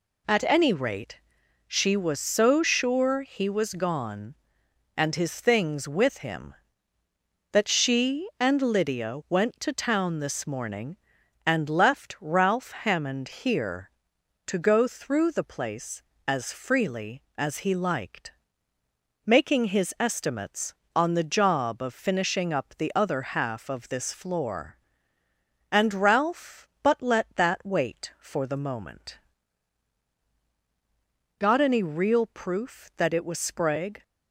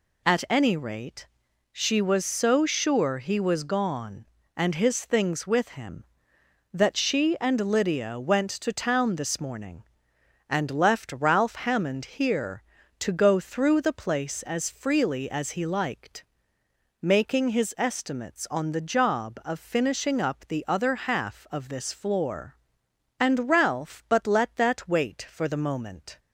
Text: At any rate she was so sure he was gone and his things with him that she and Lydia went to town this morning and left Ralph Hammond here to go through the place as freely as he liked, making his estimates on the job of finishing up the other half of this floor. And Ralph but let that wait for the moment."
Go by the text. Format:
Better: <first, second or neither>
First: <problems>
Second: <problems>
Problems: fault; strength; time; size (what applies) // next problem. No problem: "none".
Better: second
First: pauses between "rate" and "she"; noticeable; at 1.1 s; 0.48 s long // goes on to say "Got any real proof that it was Sprague"; strong; from 31.3 s on; 2.6 s long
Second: pauses between "rate" and "she"; at 1.2 s; 0.44 s long